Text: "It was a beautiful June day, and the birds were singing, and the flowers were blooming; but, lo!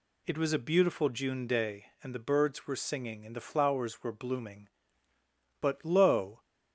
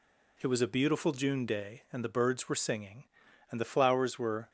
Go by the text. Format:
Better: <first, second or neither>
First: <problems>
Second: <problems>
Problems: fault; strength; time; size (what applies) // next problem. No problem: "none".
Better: first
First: none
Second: stops before "blooming but lo"; at 4.4 s